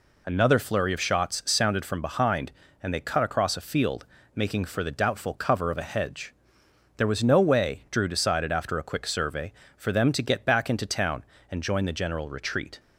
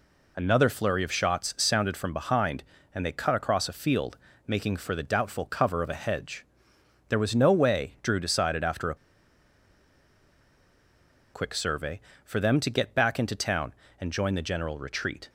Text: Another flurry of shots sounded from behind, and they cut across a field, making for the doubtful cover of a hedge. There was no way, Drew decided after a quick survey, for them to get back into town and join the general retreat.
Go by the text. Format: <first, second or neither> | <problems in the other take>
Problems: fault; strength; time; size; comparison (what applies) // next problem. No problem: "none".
first | pauses between "a" and "quick"; strong; at 8.9 s; 2.3 s long